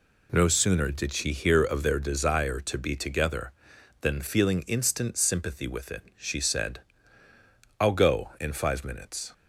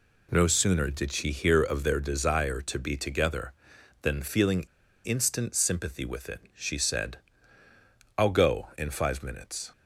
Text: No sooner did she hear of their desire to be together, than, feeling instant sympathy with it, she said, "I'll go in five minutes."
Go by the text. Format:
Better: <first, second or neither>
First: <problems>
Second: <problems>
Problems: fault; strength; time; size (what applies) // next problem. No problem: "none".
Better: first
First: none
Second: pauses between "feeling" and "instant"; at 4.6 s; 0.40 s long